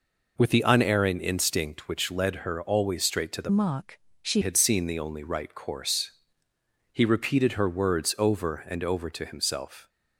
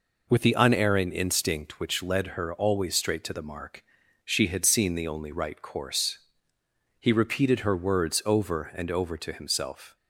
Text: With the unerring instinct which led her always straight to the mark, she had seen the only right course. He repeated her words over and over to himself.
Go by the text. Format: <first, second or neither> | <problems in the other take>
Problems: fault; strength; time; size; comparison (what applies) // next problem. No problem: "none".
second | changes voice from "mark" to "she"; from 3.5 to 4.4 s; 0.9 s long